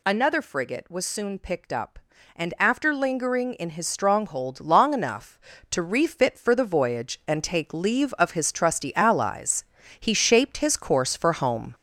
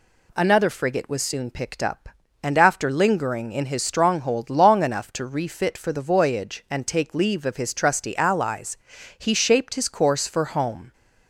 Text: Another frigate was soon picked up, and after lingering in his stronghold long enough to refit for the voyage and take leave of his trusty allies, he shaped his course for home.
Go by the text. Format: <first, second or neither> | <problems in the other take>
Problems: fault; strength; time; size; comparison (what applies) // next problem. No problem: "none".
second | gets louder; noticeable; throughout; 5 dB